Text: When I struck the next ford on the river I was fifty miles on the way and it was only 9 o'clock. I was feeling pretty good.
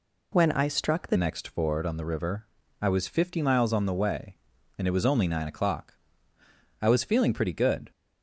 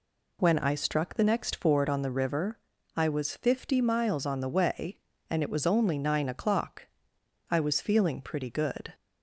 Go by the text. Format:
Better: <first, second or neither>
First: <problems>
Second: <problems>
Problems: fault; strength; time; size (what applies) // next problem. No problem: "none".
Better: second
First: changes voice at "next"; from 1.1 s on; 6.8 s long // pauses between "river" and "I"; slight; at 2.4 s; 0.34 s long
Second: pauses between "river" and "I"; slight; at 2.5 s; 0.36 s long